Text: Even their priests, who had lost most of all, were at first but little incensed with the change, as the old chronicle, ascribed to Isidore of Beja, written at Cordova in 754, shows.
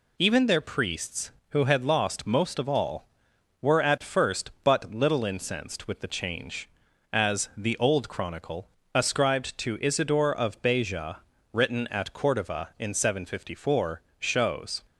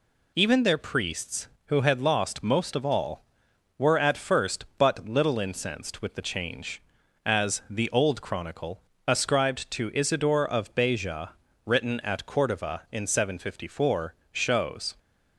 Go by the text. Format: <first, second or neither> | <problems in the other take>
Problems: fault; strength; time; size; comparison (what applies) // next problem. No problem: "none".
neither | none